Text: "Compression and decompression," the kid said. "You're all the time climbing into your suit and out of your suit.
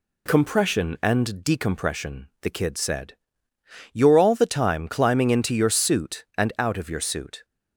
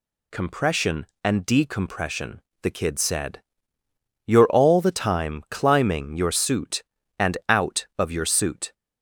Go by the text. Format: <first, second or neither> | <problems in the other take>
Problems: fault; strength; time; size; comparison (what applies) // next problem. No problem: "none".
first | skips "into"; at 6.1 s